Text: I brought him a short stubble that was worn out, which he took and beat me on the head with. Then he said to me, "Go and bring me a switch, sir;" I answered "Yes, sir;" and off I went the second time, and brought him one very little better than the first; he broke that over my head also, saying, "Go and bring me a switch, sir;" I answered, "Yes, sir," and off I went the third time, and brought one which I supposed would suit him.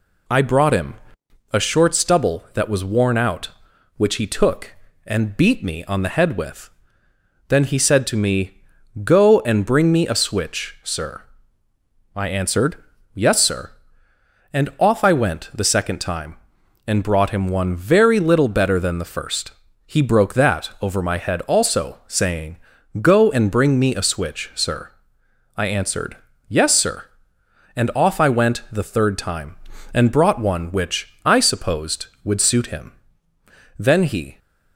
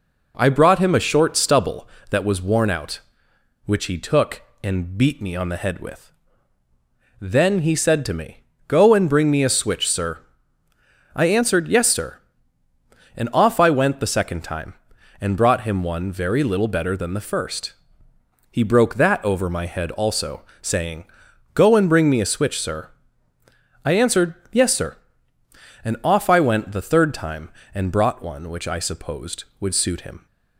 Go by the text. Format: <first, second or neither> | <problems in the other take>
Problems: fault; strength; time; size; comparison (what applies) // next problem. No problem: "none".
second | pauses between "him" and "a"; noticeable; at 0.9 s; 0.58 s long // pauses between "answered" and "Yes"; at 12.7 s; 0.38 s long // goes on to say "Then he"; from 33.7 s on; 0.60 s long